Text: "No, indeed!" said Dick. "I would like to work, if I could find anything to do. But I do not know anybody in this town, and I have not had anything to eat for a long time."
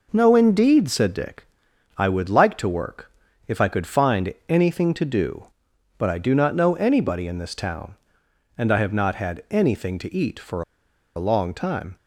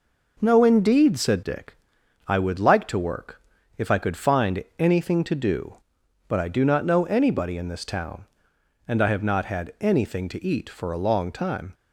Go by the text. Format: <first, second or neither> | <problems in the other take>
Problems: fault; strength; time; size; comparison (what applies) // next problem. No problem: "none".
second | pauses between "for" and "a"; noticeable; at 10.6 s; 0.54 s long